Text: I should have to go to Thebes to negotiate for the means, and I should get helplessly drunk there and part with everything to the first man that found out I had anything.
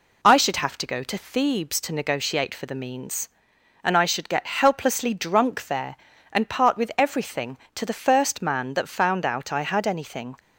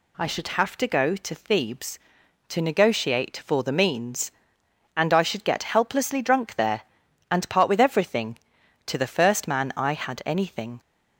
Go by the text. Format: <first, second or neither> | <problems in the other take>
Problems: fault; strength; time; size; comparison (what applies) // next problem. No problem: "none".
first | skips "that found out"; at 9.7 s